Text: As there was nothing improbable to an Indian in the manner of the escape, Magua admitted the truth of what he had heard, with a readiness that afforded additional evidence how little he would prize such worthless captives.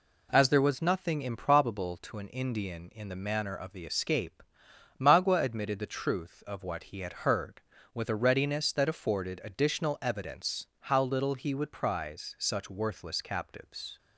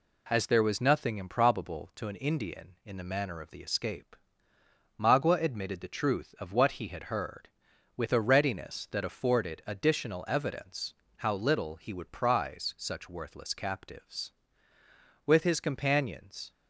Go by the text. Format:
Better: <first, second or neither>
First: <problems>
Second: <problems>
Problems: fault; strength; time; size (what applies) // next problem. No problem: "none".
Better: first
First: none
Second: pauses between "evidence" and "how"; slight; at 10.9 s; 0.24 s long // goes on to say "With his companions"; noticeable; from 15.2 s on; 1.2 s long